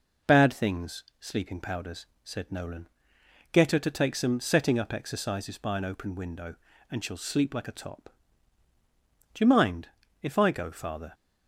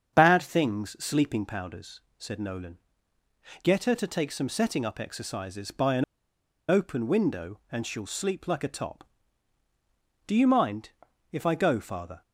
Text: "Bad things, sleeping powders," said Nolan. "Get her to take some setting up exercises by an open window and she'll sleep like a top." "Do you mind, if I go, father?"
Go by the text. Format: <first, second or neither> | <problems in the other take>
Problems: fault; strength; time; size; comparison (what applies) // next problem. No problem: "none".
first | starts louder than the rest; strong; until 1.2 s; 7.5 dB // pauses between "an" and "open"; noticeable; at 6.0 s; 0.65 s long